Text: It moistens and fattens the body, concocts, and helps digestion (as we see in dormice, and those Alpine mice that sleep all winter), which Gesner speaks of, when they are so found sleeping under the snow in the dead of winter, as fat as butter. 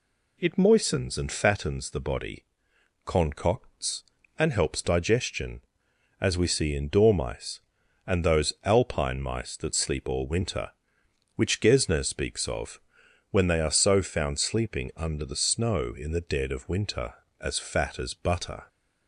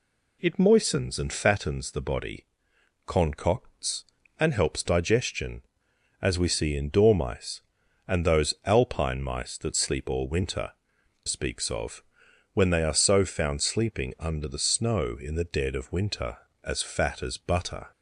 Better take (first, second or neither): first